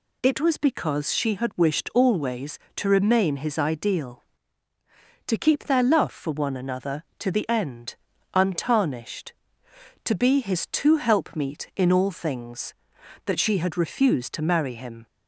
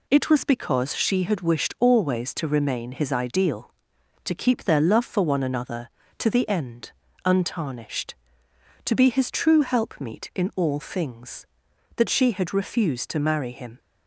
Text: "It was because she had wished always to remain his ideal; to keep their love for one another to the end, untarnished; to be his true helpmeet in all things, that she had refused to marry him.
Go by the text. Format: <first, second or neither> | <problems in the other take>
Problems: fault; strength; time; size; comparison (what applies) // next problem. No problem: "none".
second | says "two" for "true"; at 10.6 s